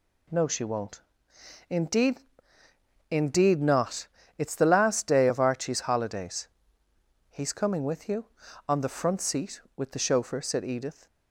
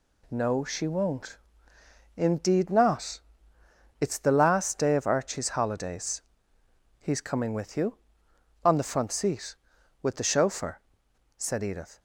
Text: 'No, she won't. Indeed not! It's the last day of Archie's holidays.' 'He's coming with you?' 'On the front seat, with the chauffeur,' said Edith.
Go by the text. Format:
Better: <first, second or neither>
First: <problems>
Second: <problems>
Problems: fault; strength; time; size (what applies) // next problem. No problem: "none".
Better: second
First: says "Indeed" twice; at 3.0 s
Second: none